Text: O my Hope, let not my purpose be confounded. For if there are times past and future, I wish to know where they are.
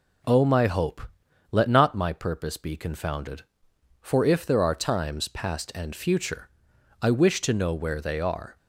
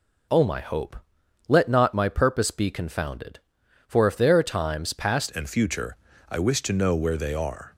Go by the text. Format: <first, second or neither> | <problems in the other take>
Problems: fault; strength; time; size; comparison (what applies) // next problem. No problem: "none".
first | changes voice at "and"; from 5.3 s on; 2.4 s long